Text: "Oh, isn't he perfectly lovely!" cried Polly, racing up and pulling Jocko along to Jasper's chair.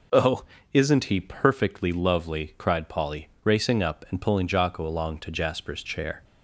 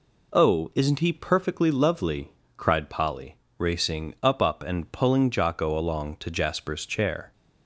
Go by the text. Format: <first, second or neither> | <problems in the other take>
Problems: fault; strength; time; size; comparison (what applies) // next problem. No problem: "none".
first | says "up" twice; at 4.4 s